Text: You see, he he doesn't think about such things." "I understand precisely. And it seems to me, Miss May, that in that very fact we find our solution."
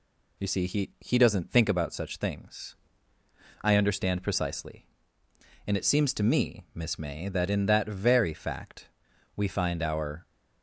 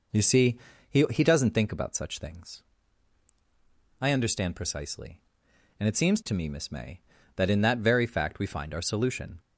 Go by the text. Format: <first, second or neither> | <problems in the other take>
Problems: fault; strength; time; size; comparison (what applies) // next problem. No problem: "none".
second | pauses between "fact" and "we"; noticeable; at 8.8 s; 0.48 s long // stops before "solution"; at 10.2 s